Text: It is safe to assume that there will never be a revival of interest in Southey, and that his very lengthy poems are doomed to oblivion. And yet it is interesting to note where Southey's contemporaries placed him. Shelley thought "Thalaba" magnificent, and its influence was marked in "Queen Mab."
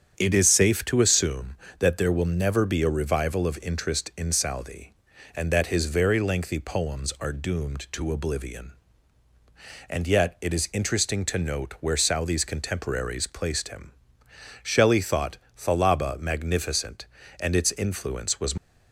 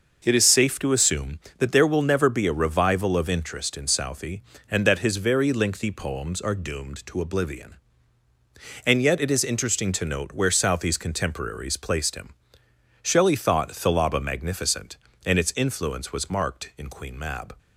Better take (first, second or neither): second